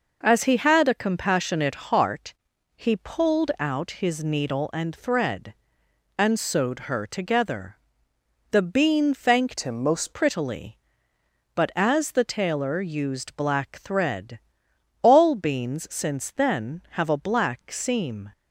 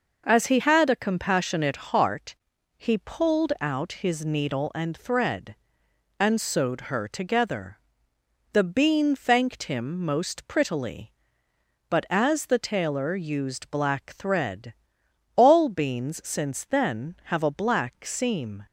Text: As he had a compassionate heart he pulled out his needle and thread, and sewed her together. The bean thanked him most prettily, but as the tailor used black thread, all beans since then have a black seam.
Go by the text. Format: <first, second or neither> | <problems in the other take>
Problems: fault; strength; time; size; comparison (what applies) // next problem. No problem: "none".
second | pauses between "heart" and "he"; at 2.3 s; 0.42 s long; also in the second // changes voice from "him" to "most"; from 9.6 to 10.1 s; 0.5 s long